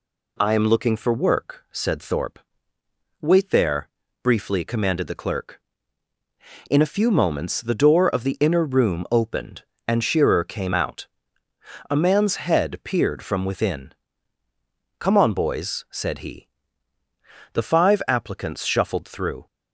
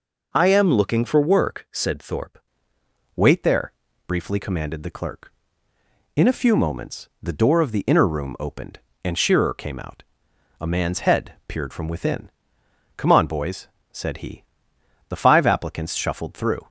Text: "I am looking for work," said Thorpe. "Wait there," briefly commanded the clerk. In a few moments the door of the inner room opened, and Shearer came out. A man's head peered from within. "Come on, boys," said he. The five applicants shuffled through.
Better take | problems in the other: first | changes voice at "Wait"; from 3.1 s on; 13.5 s long

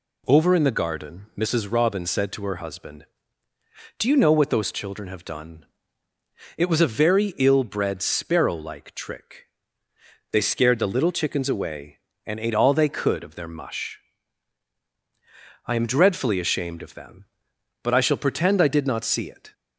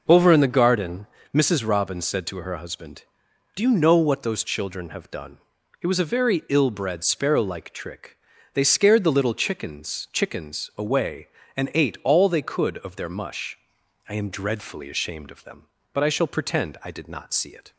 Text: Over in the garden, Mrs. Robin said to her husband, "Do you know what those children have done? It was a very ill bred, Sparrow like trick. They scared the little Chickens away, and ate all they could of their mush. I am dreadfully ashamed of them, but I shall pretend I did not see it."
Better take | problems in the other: first | says "Chickens" twice; at 10.1 s

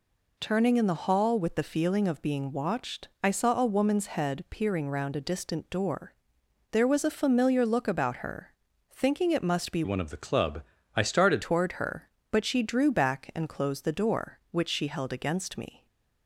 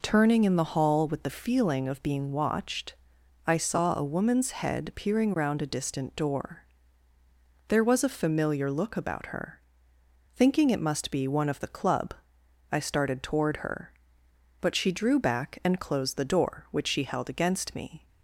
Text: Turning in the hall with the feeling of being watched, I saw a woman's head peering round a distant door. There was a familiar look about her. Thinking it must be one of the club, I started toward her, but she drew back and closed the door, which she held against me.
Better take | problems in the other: second | changes voice from "one" to "started"; from 9.8 to 11.4 s; 1.6 s long

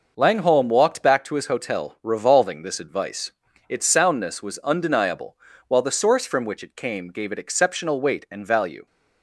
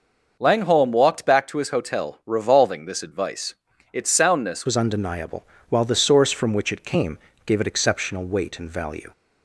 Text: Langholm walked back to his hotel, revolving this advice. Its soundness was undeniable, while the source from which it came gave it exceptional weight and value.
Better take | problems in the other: first | starts louder than the rest; noticeable; until 1.4 s; 6 dB // changes voice at "was"; from 4.6 s on; 4.5 s long // pauses between "came" and "gave"; slight; at 7.1 s; 0.28 s long

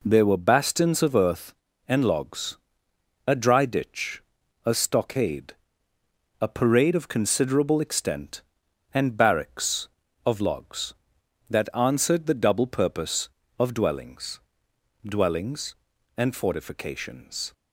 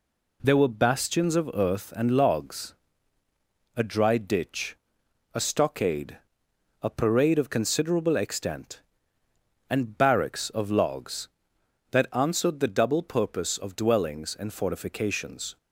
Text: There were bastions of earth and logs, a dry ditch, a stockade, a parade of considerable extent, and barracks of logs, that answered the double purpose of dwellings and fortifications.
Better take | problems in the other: second | says "dwellings" twice; at 15.0 s

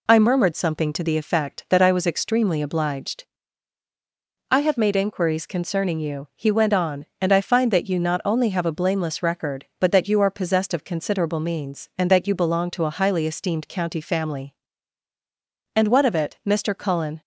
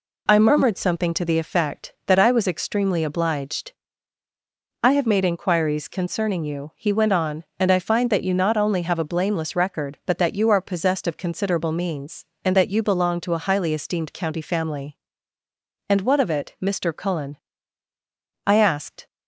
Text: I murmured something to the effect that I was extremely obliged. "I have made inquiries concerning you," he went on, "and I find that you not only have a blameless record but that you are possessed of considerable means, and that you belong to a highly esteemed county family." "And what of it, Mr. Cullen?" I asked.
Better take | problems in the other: second | stops before "I asked"; at 17.2 s

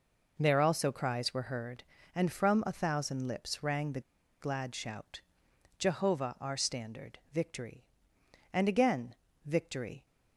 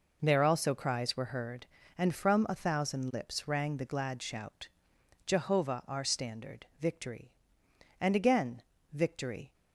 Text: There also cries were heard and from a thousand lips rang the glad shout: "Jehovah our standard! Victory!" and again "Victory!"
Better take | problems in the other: second | pauses between "the" and "glad"; at 3.9 s; 0.40 s long // pauses between "again" and "Victory"; slight; at 9.1 s; 0.30 s long; slight in the second

